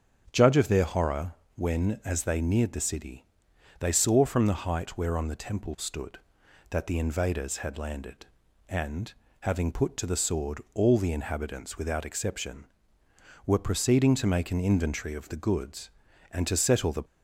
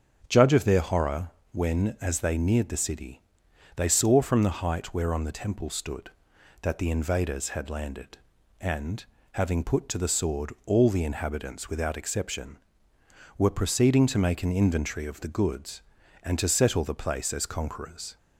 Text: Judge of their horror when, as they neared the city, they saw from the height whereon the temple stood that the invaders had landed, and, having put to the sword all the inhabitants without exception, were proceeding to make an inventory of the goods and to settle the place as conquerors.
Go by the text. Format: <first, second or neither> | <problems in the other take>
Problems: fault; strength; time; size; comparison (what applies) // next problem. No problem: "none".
second | starts louder than the rest; strong; until 1.3 s; 7 dB; strong in the second // pauses between "horror" and "when"; slight; at 1.3 s; 0.22 s long; slight in the second // stops before "place as conquerors"; at 17.0 s